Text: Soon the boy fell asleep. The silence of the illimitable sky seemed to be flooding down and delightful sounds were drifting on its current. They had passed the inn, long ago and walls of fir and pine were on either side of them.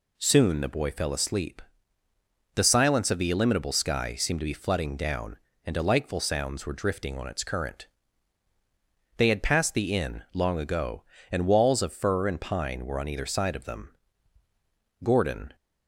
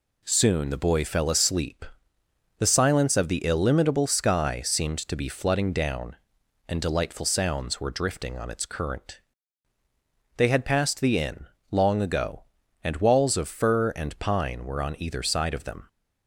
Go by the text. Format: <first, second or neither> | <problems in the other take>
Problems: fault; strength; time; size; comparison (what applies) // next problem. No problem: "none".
second | goes on to say "Gordon"; from 15.0 s on; 0.52 s long